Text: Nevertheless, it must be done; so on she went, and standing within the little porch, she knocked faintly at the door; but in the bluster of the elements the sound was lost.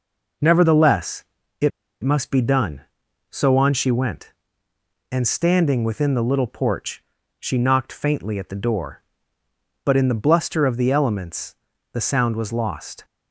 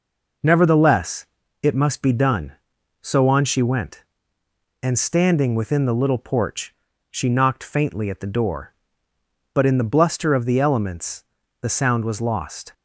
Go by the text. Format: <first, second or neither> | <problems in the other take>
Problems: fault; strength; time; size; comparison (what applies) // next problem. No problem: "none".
second | pauses between "it" and "must"; slight; at 1.7 s; 0.33 s long // pauses between "elements" and "the"; slight; at 11.5 s; 0.36 s long; slight in the second